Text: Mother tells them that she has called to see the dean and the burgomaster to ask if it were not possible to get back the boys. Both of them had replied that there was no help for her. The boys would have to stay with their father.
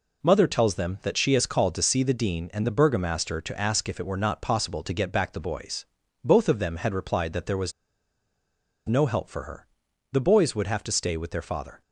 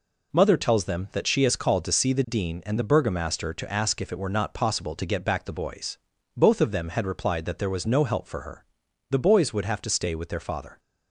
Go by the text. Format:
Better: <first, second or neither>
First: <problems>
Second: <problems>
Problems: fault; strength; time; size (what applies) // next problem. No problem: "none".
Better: second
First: pauses between "was" and "no"; at 7.7 s; 1.1 s long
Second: none